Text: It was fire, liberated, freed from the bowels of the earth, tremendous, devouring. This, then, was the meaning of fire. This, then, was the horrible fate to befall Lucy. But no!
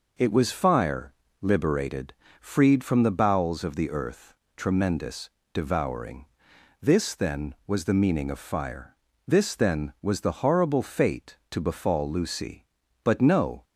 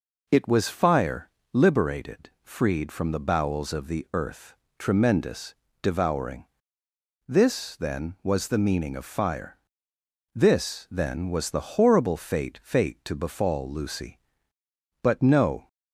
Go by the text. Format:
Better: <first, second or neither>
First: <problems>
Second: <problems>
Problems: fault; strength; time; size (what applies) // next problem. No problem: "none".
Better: first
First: none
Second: says "fate" twice; at 12.6 s